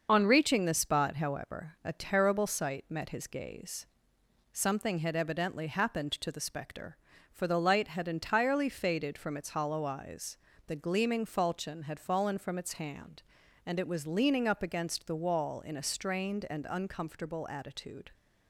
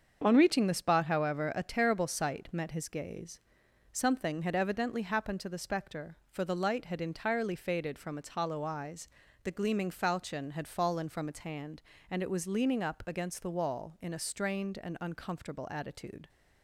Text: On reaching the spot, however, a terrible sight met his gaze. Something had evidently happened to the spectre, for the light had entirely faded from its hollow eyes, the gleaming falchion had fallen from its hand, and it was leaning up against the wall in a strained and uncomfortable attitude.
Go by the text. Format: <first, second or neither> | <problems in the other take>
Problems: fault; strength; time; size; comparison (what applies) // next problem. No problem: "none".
second | loses the start of "On"; at 0.0 s; 30 ms // starts louder than the rest; until 1.1 s; 6.5 dB; also in the second